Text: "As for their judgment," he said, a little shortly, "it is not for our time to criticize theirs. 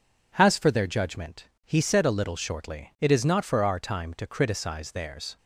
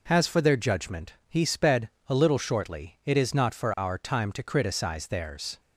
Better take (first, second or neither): first